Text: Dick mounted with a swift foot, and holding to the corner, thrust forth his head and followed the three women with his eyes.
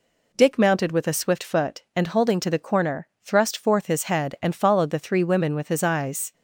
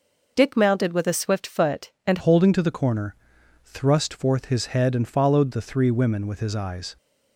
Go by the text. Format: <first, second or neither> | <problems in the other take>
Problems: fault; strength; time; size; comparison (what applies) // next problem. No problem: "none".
first | changes voice at "holding"; from 2.1 s on; 4.8 s long